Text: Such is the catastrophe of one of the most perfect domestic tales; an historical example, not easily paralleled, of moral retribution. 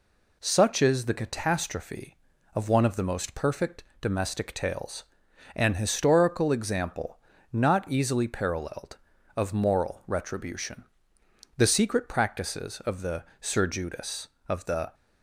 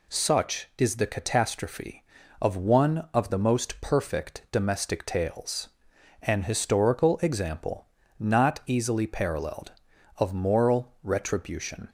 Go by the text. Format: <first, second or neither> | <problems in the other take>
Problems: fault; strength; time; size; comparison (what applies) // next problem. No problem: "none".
second | pauses between "perfect" and "domestic"; slight; at 3.8 s; 0.16 s long // goes on to say "The secret practices of the Sir Judas of the"; strong; from 11.5 s on; 3.3 s long